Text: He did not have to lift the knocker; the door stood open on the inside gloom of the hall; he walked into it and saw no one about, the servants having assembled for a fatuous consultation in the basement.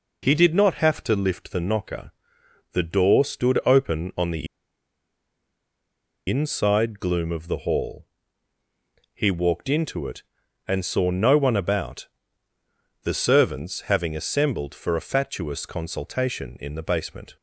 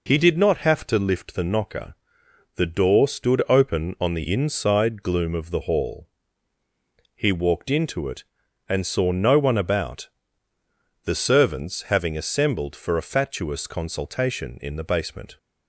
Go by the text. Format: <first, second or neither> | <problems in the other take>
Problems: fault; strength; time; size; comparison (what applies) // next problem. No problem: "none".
second | pauses between "the" and "inside"; strong; at 4.4 s; 1.8 s long